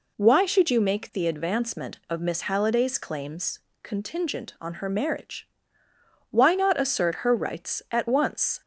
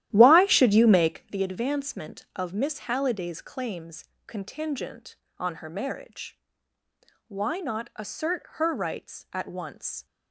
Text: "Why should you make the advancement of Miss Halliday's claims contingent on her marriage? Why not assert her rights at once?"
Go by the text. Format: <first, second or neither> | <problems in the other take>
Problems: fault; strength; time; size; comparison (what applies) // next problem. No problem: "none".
first | starts louder than the rest; strong; until 1.3 s; 13 dB // pauses between "claims" and "contingent"; slight; at 4.0 s; 0.24 s long; slight in the first